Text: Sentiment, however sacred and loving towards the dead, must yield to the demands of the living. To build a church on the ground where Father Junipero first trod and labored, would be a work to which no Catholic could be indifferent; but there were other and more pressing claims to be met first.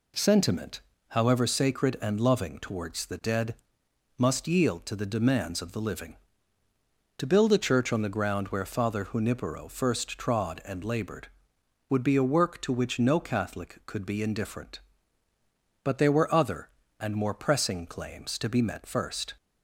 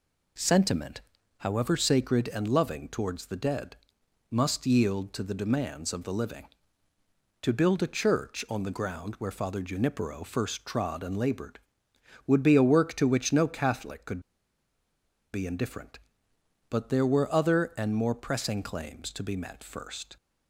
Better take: first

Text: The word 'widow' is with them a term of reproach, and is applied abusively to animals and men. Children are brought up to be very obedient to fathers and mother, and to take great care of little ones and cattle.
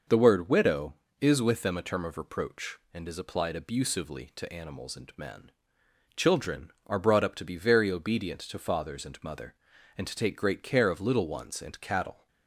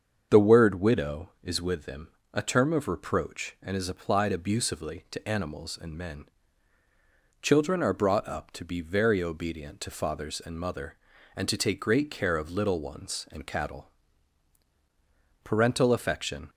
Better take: first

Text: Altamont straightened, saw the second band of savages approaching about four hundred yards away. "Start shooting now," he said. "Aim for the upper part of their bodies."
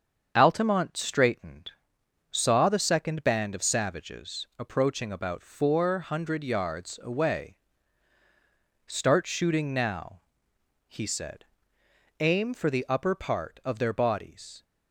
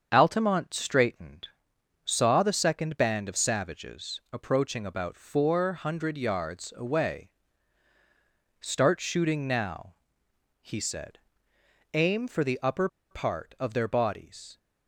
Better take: first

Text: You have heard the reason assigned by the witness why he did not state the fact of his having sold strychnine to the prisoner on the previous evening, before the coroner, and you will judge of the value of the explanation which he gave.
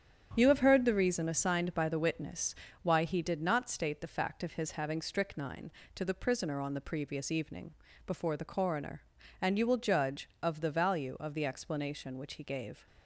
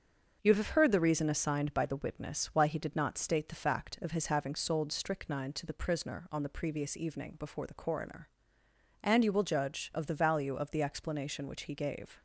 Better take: second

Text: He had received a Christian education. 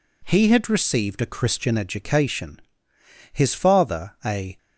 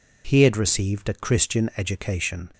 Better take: second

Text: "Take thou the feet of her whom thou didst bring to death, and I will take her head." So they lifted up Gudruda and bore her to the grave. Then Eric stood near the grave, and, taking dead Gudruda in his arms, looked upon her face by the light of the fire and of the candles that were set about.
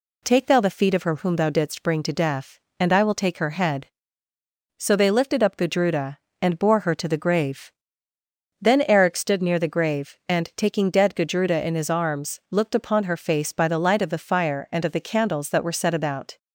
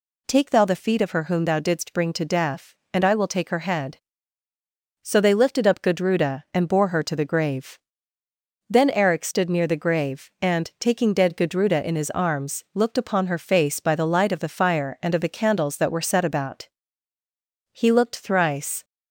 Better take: first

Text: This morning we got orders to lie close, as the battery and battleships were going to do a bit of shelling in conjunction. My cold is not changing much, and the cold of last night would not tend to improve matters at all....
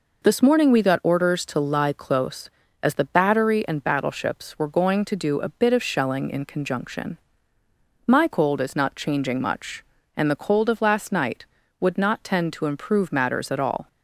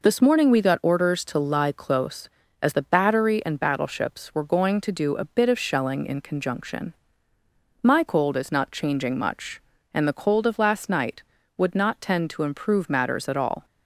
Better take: neither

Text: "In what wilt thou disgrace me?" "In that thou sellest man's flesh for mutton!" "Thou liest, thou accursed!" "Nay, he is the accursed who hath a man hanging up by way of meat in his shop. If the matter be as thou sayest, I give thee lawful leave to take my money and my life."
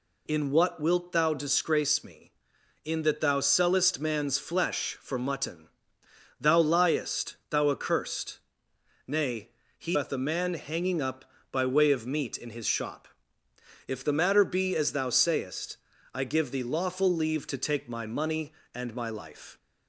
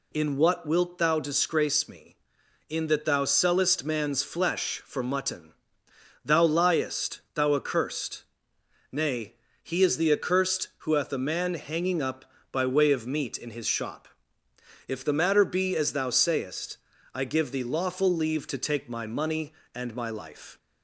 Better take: second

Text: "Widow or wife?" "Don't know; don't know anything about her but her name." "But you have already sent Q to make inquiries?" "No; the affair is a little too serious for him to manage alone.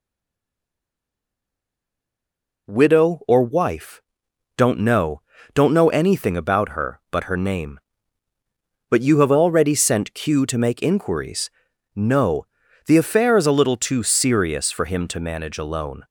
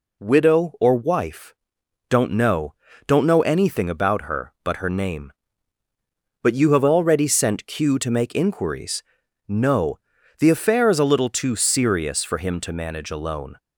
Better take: second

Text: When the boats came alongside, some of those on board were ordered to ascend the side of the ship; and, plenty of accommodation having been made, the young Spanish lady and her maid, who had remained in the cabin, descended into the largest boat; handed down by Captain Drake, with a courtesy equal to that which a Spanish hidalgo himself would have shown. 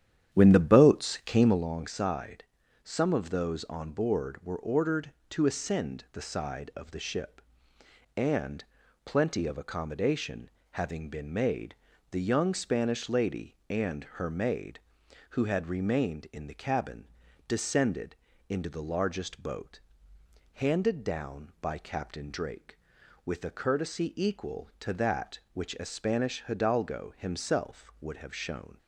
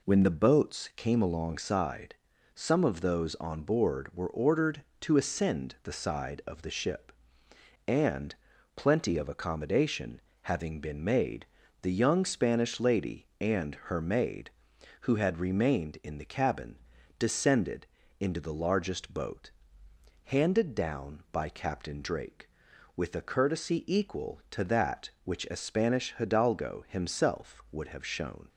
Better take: second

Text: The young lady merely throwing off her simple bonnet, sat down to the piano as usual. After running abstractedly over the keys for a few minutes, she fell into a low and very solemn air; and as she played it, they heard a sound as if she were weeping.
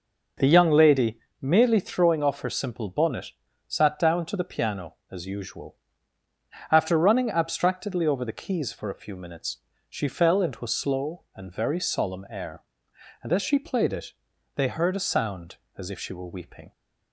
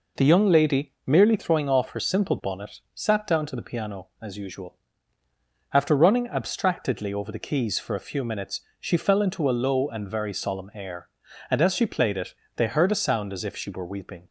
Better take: second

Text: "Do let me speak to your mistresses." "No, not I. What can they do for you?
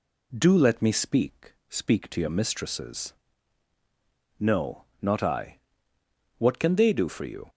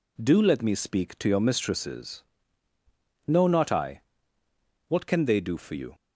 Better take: second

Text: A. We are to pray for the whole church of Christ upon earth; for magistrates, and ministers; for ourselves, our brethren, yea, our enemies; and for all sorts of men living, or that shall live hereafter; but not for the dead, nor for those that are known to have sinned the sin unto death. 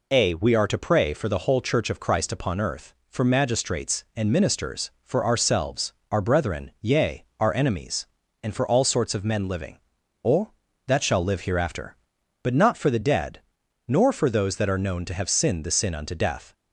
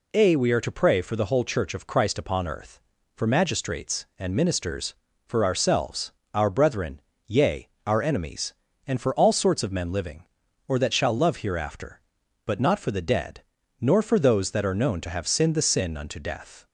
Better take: first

